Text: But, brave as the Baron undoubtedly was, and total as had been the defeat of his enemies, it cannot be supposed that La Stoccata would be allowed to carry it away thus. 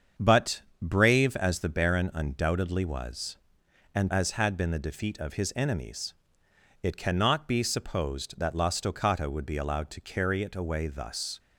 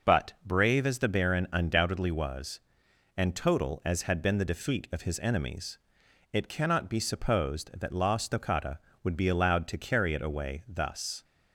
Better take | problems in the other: second | starts louder than the rest; strong; until 1.4 s; 7 dB // skips "total"; at 4.1 s

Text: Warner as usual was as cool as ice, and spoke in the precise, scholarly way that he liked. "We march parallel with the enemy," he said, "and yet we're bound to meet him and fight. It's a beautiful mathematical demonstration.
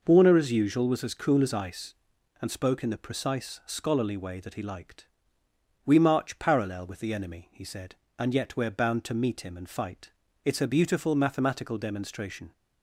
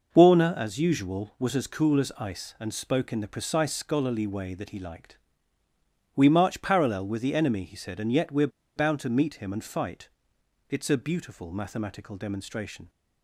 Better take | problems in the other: first | pauses between "we're" and "bound"; slight; at 8.4 s; 0.27 s long

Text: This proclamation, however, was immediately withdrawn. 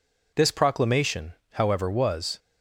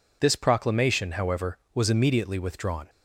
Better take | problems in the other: second | stops before "immediately withdrawn"; at 2.3 s

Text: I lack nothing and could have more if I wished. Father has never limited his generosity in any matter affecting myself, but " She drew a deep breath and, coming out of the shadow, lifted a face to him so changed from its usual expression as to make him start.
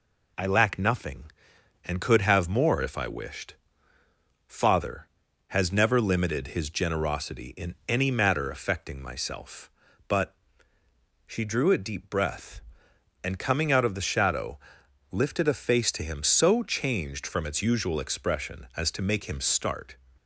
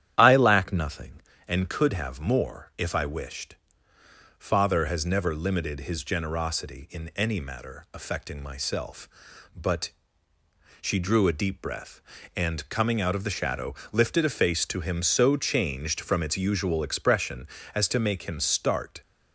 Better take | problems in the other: first | starts louder than the rest; strong; until 1.3 s; 10.5 dB

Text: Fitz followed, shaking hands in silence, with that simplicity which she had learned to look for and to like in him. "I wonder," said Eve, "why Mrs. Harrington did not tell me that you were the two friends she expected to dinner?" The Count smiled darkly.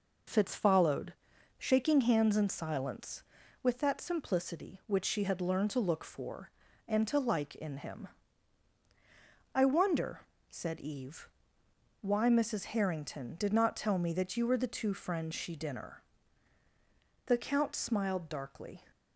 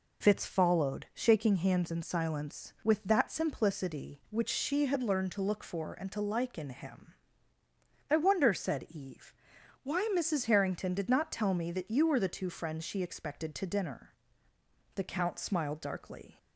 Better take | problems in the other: second | skips "expected to"; at 15.5 s

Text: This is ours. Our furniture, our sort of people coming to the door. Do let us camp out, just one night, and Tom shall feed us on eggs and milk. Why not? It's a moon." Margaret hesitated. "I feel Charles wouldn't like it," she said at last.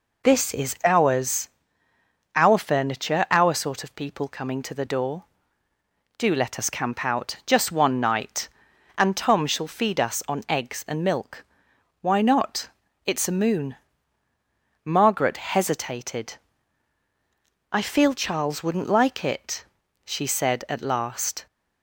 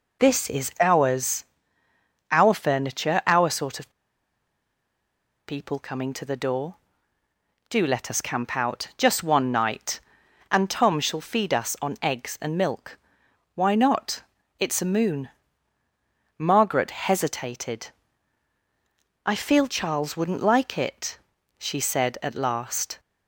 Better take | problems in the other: first | pauses between "of" and "people"; strong; at 3.9 s; 1.5 s long

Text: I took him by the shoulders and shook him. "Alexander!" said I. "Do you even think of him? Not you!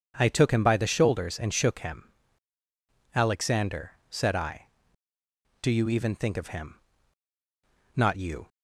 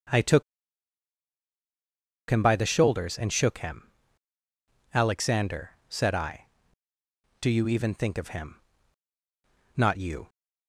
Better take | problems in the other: first | pauses between "took" and "him"; strong; at 0.4 s; 1.8 s long

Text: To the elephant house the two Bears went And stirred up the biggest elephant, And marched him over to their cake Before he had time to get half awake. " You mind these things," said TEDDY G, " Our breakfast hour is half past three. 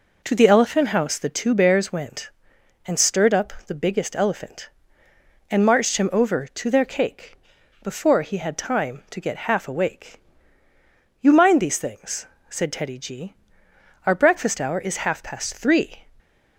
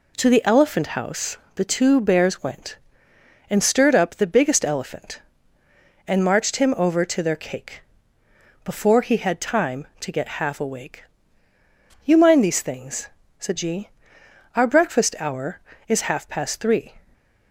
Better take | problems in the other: first | pauses between "house" and "the"; slight; at 1.3 s; 0.20 s long // pauses between "cake" and "Before"; noticeable; at 7.8 s; 0.82 s long; noticeable in the first // skips "TEDDY"; at 13.5 s // stays silent after the last word; slight; from 17.0 s on; 0.5 s long

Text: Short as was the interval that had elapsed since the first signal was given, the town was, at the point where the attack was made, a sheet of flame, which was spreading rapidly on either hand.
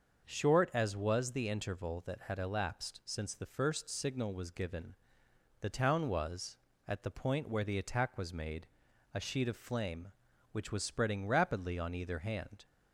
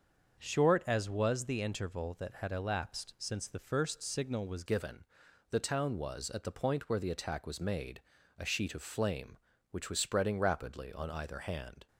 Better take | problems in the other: first | starts louder than the rest; until 1.4 s; 6.5 dB; also in the first // changes voice at "given"; from 4.6 s on; 7.2 s long

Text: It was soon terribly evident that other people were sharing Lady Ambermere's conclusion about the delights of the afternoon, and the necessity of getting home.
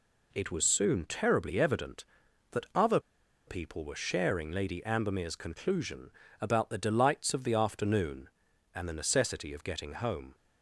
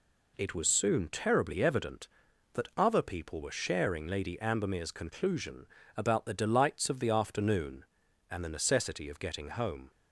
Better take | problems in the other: second | pauses between "other" and "people"; noticeable; at 2.9 s; 0.47 s long // pauses between "conclusion" and "about"; slight; at 6.1 s; 0.30 s long; slight in the second

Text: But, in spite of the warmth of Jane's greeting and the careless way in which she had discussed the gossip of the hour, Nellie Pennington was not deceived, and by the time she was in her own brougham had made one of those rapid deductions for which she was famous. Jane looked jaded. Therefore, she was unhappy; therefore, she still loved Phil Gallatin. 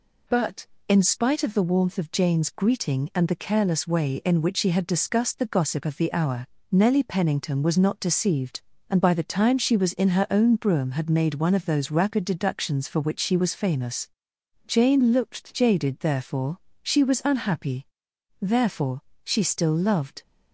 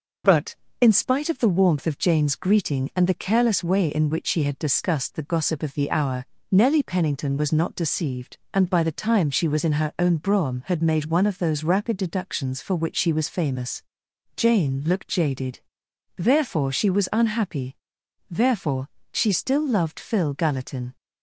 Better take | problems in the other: second | stops before "Phil Gallatin"; at 20.2 s

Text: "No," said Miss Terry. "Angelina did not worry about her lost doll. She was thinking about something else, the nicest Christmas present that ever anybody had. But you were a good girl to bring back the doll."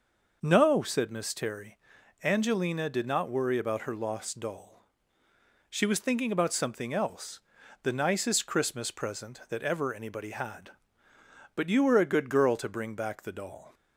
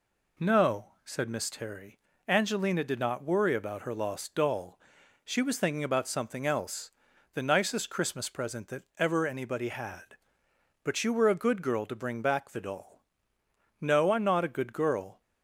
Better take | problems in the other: first | goes on to say "No I'm not a good girl"; from 13.7 s on; 1.4 s long

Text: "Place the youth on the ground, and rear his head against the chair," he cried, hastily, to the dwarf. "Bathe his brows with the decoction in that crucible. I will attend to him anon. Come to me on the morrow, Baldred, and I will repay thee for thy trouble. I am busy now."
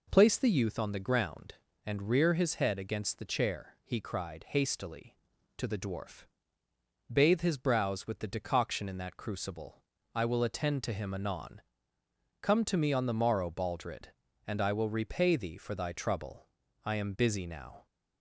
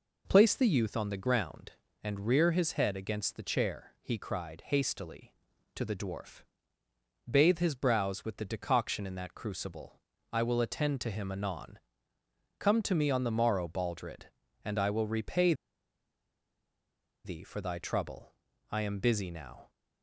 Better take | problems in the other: first | pauses between "repay" and "thee"; strong; at 15.5 s; 1.7 s long

